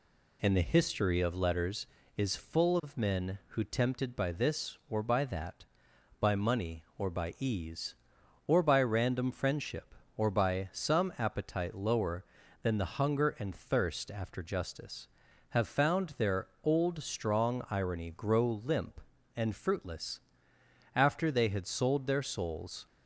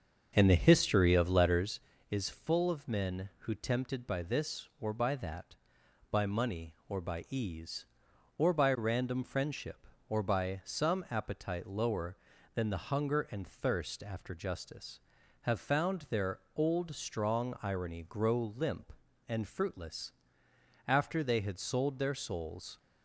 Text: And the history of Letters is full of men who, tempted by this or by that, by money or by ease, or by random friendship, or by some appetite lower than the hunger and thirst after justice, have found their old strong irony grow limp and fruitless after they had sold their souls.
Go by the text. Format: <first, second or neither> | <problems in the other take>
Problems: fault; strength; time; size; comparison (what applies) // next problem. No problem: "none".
first | starts louder than the rest; until 1.8 s; 6.5 dB // pauses between "their" and "old"; slight; at 16.3 s; 0.18 s long; slight in the first // pauses between "fruitless" and "after"; noticeable; at 20.1 s; 0.74 s long; noticeable in the first